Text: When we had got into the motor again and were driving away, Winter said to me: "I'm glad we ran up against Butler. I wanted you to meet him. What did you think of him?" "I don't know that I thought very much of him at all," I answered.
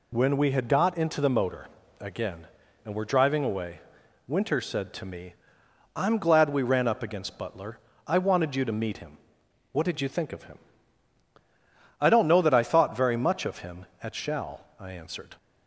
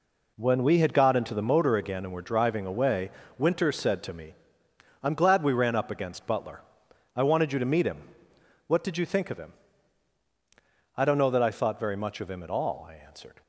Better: second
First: pauses between "motor" and "again"; slight; at 1.6 s; 0.34 s long // says "shall" for "all"; at 14.1 s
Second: none

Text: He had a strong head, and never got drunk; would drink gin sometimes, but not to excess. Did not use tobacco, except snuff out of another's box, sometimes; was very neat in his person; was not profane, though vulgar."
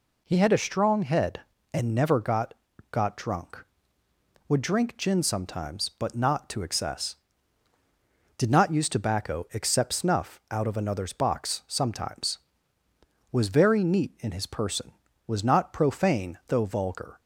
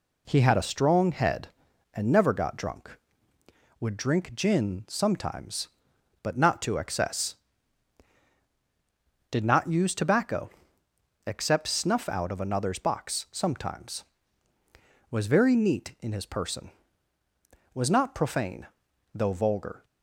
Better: second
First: says "got" twice; at 2.9 s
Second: none

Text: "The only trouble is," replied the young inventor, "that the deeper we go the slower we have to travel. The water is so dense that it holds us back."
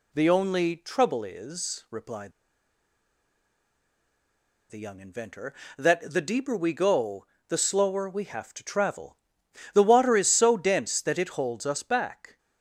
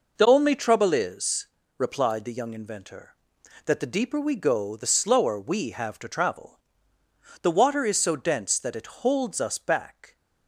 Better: second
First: pauses between "replied" and "the"; strong; at 2.3 s; 2.3 s long // pauses between "go" and "the"; slight; at 7.2 s; 0.20 s long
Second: none

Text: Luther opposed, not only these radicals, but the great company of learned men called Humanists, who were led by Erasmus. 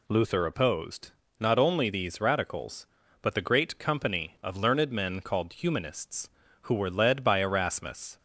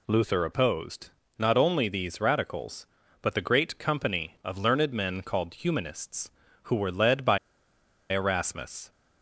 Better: first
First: none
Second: pauses between "by" and "Erasmus"; noticeable; at 7.3 s; 0.73 s long

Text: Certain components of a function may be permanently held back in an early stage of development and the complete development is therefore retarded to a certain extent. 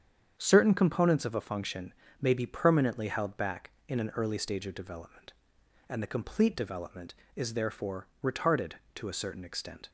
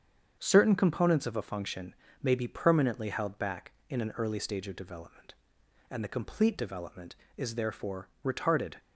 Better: first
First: starts louder than the rest; strong; until 1.3 s; 8 dB // pauses between "function" and "may"; slight; at 1.9 s; 0.26 s long // pauses between "therefore" and "retarded"; slight; at 8.0 s; 0.16 s long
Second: starts louder than the rest; strong; until 1.4 s; 7.5 dB // pauses between "function" and "may"; slight; at 1.9 s; 0.26 s long // pauses between "therefore" and "retarded"; slight; at 8.0 s; 0.16 s long // stops before "to a certain extent"; at 8.7 s

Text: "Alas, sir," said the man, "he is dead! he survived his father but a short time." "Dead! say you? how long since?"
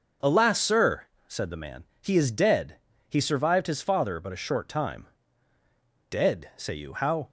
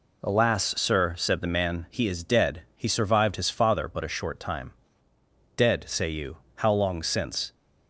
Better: second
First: starts louder than the rest; until 1.4 s; 6.5 dB // stops before "long since"; at 7.2 s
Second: none

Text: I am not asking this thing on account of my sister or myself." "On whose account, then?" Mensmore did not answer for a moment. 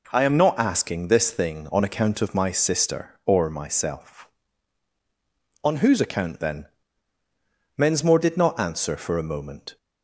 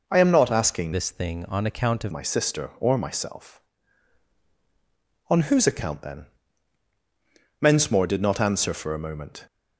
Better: first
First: none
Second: changes voice from "this" to "of"; from 0.9 to 2.1 s; 1.2 s long

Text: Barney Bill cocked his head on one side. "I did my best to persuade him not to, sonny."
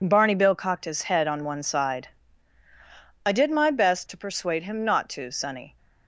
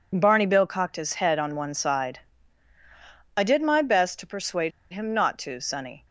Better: first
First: none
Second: pauses between "persuade" and "him"; slight; at 4.7 s; 0.22 s long

